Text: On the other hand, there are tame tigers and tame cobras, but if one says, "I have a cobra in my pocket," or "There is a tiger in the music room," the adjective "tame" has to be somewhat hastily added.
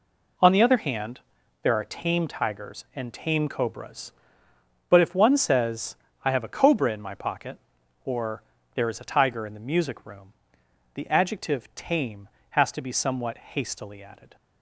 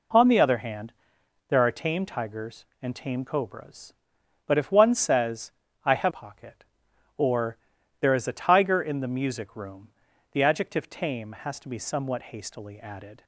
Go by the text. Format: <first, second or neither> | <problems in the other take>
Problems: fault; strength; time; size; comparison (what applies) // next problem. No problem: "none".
first | skips "a cobra in my"; at 6.1 s // pauses between "or" and "There"; at 7.5 s; 0.44 s long; slight in the first